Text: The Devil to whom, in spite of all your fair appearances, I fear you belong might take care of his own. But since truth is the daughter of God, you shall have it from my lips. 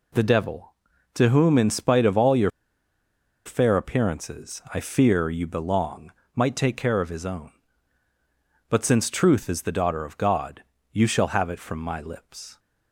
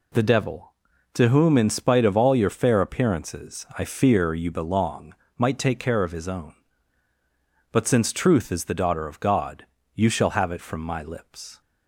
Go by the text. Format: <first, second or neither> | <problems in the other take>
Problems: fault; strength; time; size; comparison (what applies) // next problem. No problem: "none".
second | pauses between "your" and "fair"; noticeable; at 2.4 s; 0.96 s long // pauses between "belong" and "might"; slight; at 6.1 s; 0.24 s long; slight in the second